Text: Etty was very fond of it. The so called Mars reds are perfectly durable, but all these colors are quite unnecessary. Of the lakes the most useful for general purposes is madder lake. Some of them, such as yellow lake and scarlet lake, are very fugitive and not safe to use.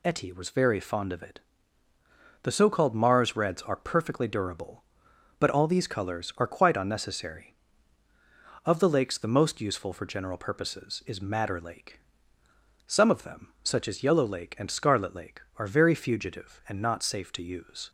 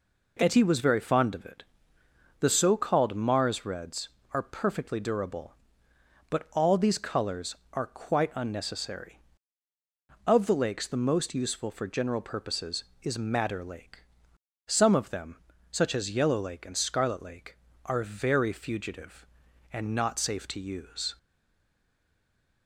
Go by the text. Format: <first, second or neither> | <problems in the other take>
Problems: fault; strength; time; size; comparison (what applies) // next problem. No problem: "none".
first | stays silent after the last word; noticeable; from 21.1 s on; 1.5 s long